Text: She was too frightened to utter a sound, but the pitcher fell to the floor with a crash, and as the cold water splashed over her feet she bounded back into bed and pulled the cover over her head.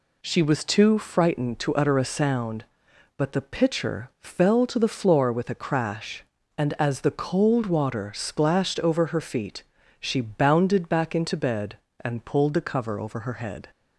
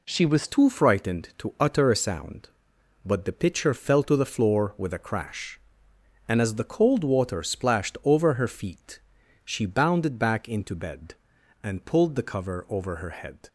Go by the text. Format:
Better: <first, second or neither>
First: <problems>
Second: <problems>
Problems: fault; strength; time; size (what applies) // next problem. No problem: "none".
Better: first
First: pauses between "feet" and "she"; slight; at 9.6 s; 0.34 s long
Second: changes voice at "too"; from 0.4 s on; 13.0 s long // pauses between "feet" and "she"; noticeable; at 8.9 s; 0.46 s long